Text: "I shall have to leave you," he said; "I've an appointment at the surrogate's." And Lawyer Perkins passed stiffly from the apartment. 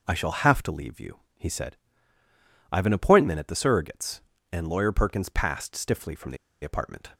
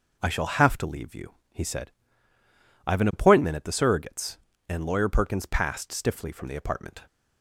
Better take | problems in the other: second | pauses between "the" and "apartment"; slight; at 6.3 s; 0.26 s long

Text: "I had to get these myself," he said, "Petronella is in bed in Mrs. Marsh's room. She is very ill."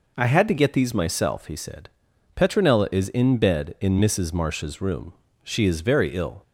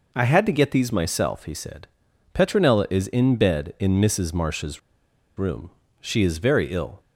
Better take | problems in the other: first | pauses between "Marsh's" and "room"; noticeable; at 4.7 s; 0.57 s long

